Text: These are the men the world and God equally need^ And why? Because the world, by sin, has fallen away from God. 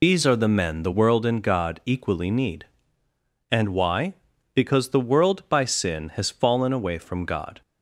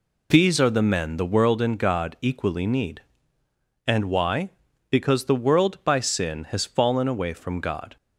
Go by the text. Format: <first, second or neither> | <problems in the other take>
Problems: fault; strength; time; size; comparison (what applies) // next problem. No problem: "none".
second | loses the start of "These"; at 0.0 s; 60 ms